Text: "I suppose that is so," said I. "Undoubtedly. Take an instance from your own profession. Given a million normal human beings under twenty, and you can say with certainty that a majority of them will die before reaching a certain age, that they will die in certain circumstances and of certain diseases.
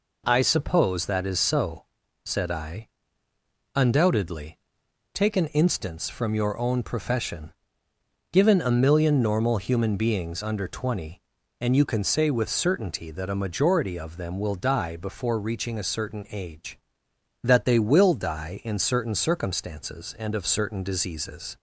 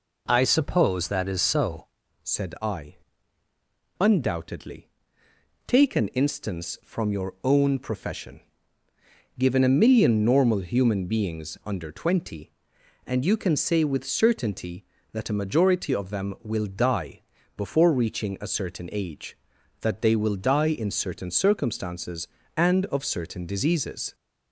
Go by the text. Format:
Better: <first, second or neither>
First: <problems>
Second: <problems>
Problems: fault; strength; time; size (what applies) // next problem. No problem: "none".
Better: first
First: none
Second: changes voice at "said"; from 2.2 s on; 21.9 s long // pauses between "die" and "before"; slight; at 17.2 s; 0.34 s long